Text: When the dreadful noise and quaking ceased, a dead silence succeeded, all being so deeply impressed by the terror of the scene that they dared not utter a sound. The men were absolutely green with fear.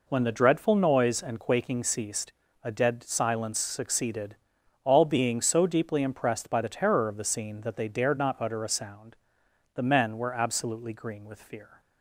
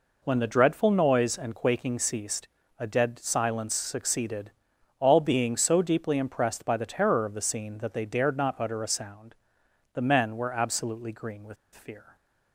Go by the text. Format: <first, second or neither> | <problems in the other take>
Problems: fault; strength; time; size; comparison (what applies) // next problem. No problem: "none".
first | pauses between "with" and "fear"; slight; at 11.5 s; 0.19 s long